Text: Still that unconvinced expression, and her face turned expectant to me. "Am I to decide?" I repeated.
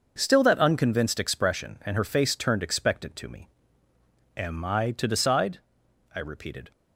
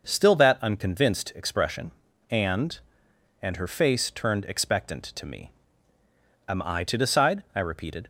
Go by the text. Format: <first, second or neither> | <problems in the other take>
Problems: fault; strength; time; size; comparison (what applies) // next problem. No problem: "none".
first | says "and" twice; at 3.4 s